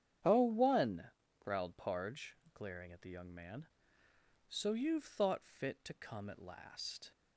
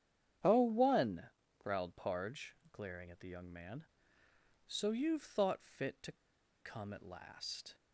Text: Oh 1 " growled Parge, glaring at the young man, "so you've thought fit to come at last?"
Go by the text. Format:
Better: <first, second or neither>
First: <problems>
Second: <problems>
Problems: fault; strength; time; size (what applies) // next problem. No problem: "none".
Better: first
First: starts louder than the rest; strong; until 1.3 s; 9 dB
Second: starts louder than the rest; strong; until 1.5 s; 9 dB // pauses between "to" and "come"; noticeable; at 6.1 s; 0.47 s long